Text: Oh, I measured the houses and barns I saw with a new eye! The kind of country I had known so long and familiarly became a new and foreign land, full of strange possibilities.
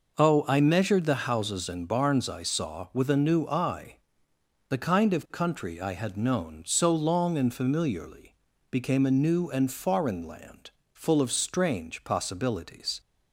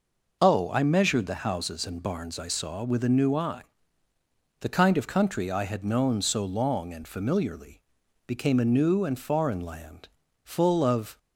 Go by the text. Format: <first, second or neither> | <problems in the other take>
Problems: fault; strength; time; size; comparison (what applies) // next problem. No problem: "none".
first | pauses between "familiarly" and "became"; at 7.8 s; 0.44 s long; also in the first // stops before "strange possibilities"; at 11.1 s